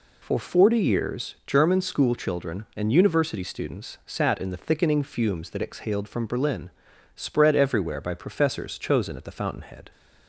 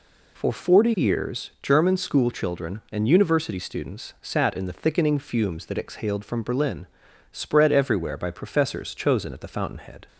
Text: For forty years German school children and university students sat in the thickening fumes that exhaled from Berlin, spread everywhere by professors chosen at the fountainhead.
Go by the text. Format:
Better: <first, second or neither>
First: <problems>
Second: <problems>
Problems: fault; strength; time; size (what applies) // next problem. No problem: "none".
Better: neither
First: none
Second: none